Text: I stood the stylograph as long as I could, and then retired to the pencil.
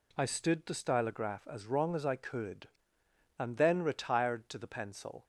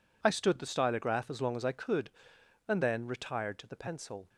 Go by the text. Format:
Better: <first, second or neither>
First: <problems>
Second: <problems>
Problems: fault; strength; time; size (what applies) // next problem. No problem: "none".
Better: second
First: says "wrong" for "long"; at 1.6 s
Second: none